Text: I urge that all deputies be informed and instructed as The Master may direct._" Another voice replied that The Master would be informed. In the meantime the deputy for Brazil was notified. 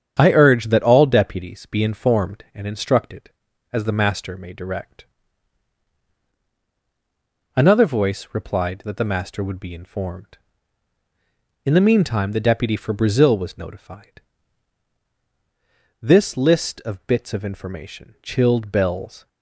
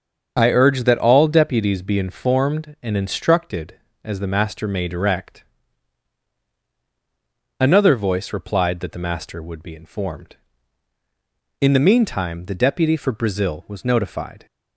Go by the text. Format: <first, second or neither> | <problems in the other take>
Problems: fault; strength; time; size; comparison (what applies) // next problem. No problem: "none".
second | starts louder than the rest; strong; until 1.2 s; 8.5 dB; also in the second // goes on to say "This list of bits of information chilled Bell's"; strong; from 16.0 s on; 3.2 s long